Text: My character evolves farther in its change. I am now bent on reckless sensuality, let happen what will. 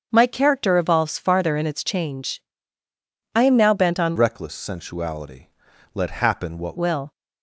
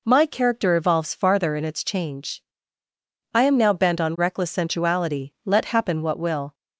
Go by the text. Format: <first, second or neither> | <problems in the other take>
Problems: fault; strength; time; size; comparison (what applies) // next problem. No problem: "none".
second | starts louder than the rest; until 1.1 s; 7 dB // changes voice from "reckless" to "what"; from 4.1 to 6.7 s; 2.6 s long